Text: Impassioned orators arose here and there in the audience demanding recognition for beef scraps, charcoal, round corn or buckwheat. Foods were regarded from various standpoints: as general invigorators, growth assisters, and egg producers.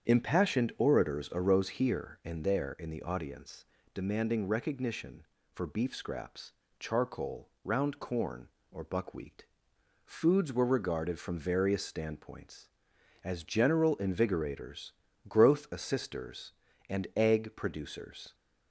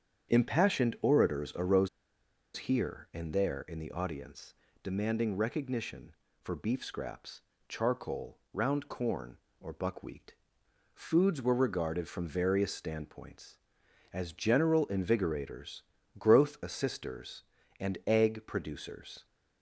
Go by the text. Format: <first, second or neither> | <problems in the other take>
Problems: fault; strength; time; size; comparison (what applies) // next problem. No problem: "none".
first | starts louder than the rest; strong; until 1.4 s; 8 dB; strong in the first // pauses between "arose" and "here"; noticeable; at 1.8 s; 0.68 s long // pauses between "audience" and "demanding"; slight; at 4.5 s; 0.28 s long; slight in the first